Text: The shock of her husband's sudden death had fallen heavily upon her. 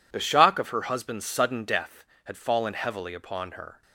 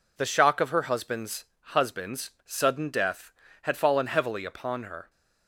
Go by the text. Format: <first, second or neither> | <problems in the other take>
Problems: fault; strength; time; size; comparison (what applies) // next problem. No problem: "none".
first | says "husband's" twice; at 1.5 s